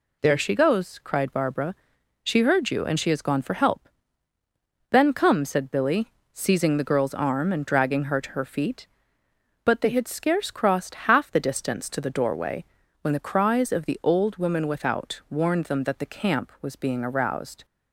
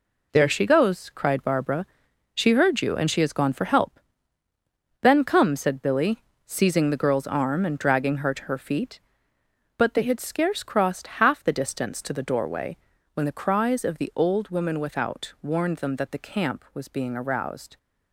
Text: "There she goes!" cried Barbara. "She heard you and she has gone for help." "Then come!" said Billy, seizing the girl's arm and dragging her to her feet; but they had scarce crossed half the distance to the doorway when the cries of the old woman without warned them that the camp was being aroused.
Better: first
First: pauses between "doorway" and "when"; at 12.6 s; 0.38 s long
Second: gets quieter; strong; throughout; 8.5 dB // pauses between "doorway" and "when"; at 12.7 s; 0.38 s long

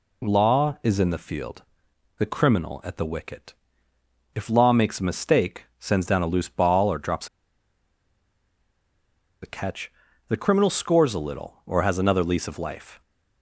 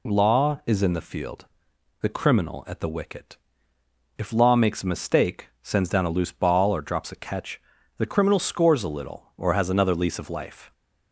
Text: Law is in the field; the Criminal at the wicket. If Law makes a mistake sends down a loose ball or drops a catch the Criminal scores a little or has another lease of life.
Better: second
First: pauses between "mistake" and "sends"; slight; at 5.6 s; 0.16 s long // pauses between "drops" and "a"; strong; at 7.2 s; 2.1 s long // pauses between "catch" and "the"; at 9.9 s; 0.38 s long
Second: pauses between "mistake" and "sends"; slight; at 5.4 s; 0.16 s long // pauses between "catch" and "the"; at 7.6 s; 0.38 s long

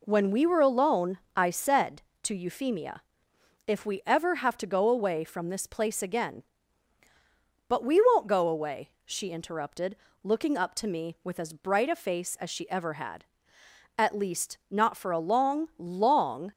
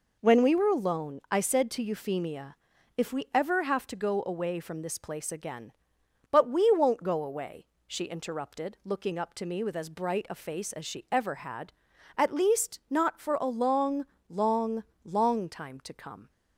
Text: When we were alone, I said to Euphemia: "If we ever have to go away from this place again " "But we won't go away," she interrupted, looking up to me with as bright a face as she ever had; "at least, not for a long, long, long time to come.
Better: second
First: stops before "long time to come"; at 16.5 s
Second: none

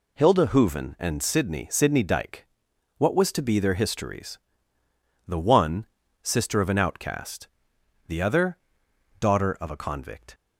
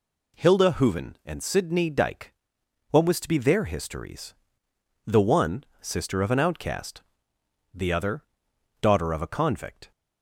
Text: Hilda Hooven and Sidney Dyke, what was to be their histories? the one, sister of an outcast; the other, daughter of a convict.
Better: second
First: says "Sidney" twice; at 1.7 s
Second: none

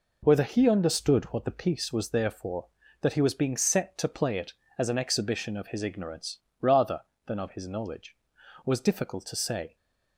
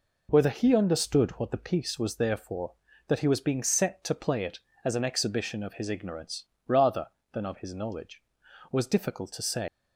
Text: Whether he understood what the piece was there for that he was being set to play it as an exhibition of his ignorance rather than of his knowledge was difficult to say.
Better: first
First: pauses between "ignorance" and "rather"; slight; at 6.3 s; 0.24 s long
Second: pauses between "ignorance" and "rather"; slight; at 6.4 s; 0.24 s long // leaves "say" unfinished; at 9.6 s; 140 ms

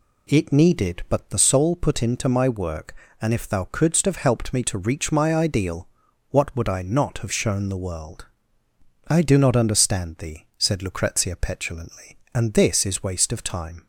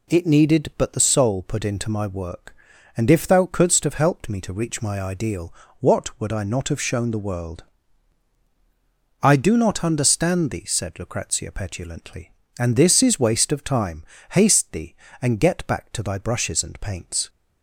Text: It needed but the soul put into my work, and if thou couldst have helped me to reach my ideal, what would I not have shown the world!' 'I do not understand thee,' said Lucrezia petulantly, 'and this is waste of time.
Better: first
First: none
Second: goes on to say "Haste thee and get back to thy brushes and paints"; strong; from 14.3 s on; 2.9 s long

